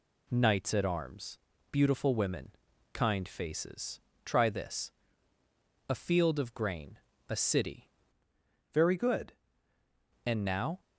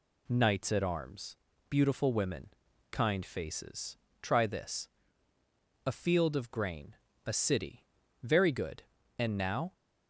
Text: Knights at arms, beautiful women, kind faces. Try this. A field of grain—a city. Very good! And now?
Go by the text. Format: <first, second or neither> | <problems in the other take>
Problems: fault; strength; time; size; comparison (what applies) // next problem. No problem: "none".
second | changes voice from "Very" to "good"; from 8.7 to 9.3 s; 0.6 s long